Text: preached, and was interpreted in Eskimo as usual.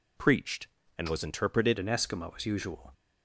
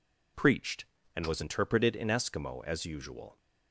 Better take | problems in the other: second | changes voice at "in"; from 1.7 s on; 1.2 s long

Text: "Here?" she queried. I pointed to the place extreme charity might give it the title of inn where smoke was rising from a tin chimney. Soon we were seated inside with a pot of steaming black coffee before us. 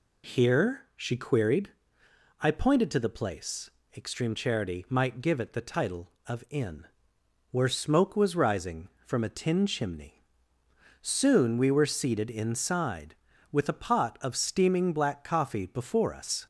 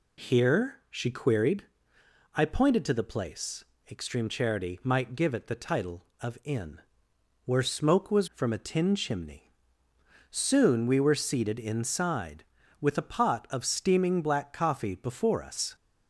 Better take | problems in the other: first | pauses between "place" and "extreme"; slight; at 3.6 s; 0.26 s long; slight in the first // pauses between "inn" and "where"; noticeable; at 6.8 s; 0.64 s long; noticeable in the first // skips "rising"; at 8.3 s

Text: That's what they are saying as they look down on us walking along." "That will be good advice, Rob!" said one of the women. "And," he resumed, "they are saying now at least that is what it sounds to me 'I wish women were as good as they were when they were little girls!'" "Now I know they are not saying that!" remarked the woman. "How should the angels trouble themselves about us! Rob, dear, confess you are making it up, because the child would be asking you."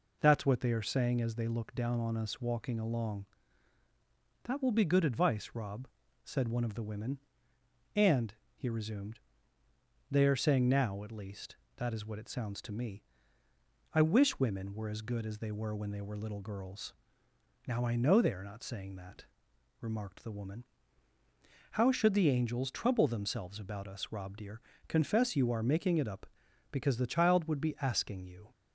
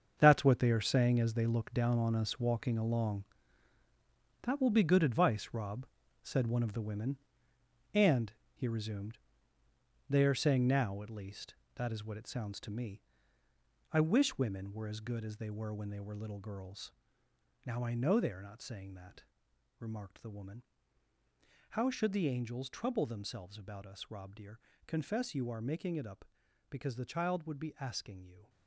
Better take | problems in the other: first | gets quieter; strong; throughout; 11 dB // pauses between "me" and "I"; noticeable; at 13.0 s; 0.88 s long; noticeable in the first

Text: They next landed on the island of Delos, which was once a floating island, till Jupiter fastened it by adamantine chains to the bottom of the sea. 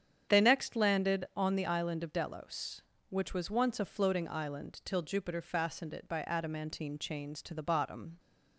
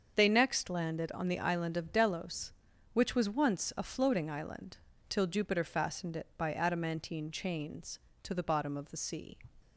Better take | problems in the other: second | starts louder than the rest; strong; until 1.4 s; 8.5 dB; also in the second // stops before "of the sea"; at 8.1 s

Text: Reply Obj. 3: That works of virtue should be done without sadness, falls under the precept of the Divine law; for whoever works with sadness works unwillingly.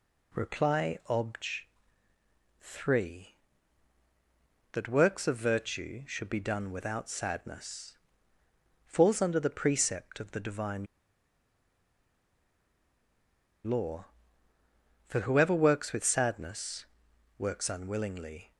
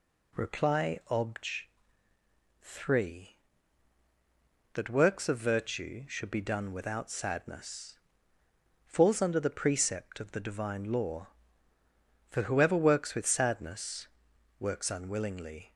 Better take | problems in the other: second | pauses between "Divine" and "law"; strong; at 10.8 s; 2.7 s long // pauses between "sadness" and "works"; noticeable; at 16.8 s; 0.50 s long; noticeable in the second

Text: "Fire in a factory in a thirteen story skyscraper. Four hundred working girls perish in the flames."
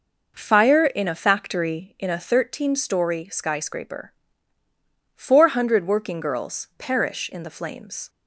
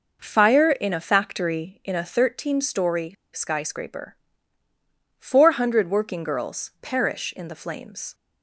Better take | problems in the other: first | pauses between "story" and "skyscraper"; slight; at 3.1 s; 0.20 s long

